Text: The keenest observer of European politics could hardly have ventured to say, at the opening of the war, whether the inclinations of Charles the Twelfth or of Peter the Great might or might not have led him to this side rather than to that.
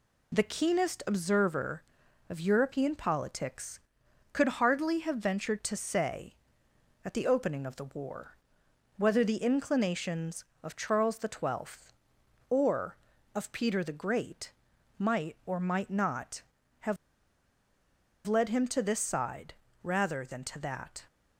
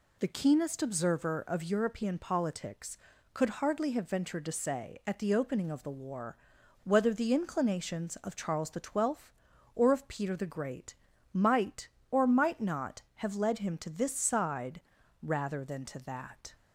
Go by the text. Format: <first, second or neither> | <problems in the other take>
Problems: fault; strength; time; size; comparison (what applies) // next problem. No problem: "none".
second | pauses between "Great" and "might"; at 14.5 s; 0.44 s long; also in the second // pauses between "have" and "led"; strong; at 16.9 s; 1.3 s long // pauses between "side" and "rather"; slight; at 19.5 s; 0.30 s long; also in the second